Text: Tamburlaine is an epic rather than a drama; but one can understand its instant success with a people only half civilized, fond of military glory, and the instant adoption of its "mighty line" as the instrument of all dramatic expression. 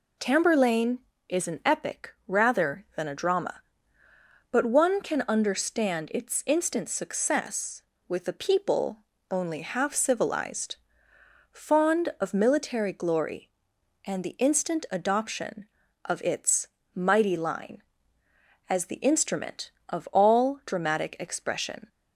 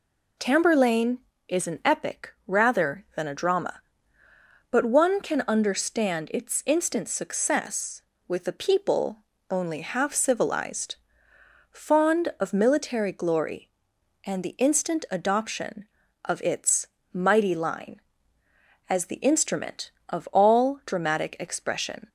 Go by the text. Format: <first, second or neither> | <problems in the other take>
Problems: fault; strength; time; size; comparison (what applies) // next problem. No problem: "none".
neither | pauses between "people" and "only"; slight; the same in both // pauses between "its" and "mighty"; slight; the same in both